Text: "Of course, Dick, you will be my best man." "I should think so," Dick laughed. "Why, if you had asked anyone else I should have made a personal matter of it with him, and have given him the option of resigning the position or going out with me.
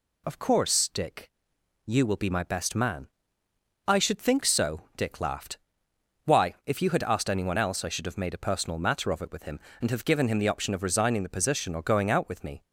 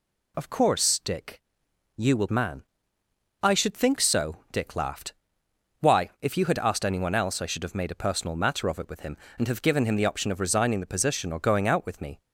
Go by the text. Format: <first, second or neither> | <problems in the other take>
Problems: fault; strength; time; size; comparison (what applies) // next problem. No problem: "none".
first | skips "be my best"; at 2.2 s